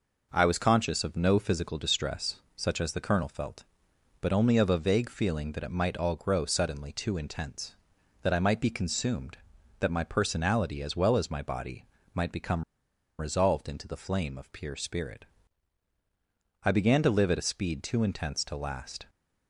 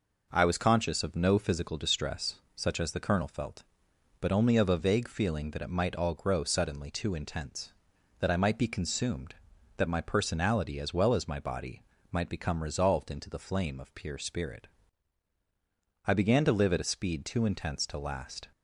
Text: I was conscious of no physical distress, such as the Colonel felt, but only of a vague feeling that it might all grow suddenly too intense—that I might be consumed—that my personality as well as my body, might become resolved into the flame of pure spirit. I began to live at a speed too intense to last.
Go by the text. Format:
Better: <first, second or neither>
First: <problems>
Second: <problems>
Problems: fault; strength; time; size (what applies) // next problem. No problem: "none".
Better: second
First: pauses between "become" and "resolved"; noticeable; at 12.6 s; 0.57 s long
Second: none